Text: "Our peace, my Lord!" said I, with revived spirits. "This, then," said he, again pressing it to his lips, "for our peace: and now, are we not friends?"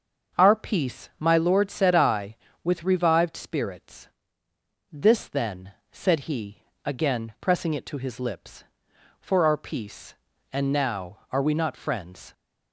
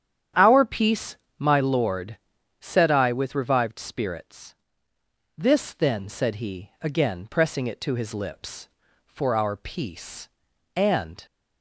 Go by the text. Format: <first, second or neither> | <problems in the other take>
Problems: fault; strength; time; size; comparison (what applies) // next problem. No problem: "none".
first | starts louder than the rest; strong; until 1.6 s; 9.5 dB; also in the first // stops before "now are we not friends"; at 11.2 s